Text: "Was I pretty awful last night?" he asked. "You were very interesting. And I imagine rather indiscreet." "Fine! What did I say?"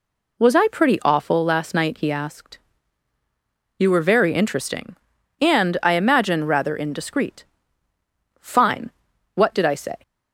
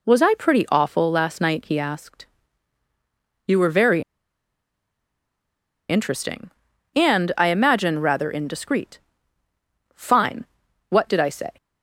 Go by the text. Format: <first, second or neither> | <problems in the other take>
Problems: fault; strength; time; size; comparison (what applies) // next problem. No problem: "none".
first | pauses between "very" and "interesting"; strong; at 4.0 s; 1.8 s long